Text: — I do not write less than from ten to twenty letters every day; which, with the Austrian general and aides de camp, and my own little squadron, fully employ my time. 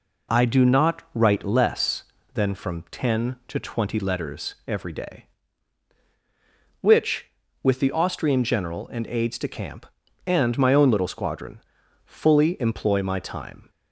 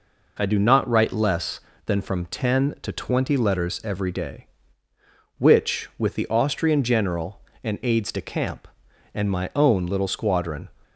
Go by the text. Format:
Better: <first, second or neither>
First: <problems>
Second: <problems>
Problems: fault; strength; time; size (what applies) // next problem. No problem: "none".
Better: first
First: none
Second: stops before "fully employ my time"; at 10.8 s